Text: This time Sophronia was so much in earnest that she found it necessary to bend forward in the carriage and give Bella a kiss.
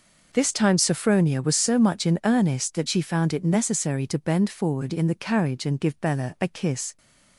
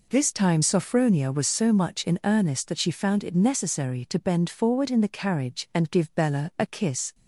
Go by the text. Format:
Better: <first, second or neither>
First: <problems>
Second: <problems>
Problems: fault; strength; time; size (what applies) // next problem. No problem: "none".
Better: neither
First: none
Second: none